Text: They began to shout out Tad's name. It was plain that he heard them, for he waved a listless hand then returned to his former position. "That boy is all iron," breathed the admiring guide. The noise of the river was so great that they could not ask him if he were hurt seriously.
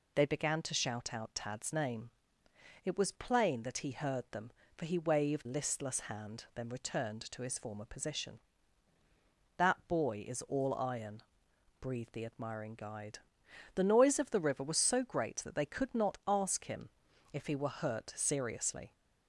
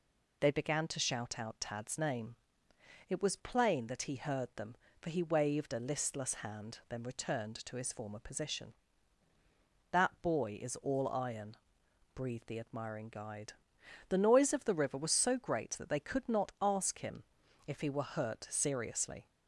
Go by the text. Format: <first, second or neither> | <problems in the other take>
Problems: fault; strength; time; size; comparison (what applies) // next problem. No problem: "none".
second | skips "a"; at 5.4 s // pauses between "him" and "if"; at 16.8 s; 0.42 s long; also in the second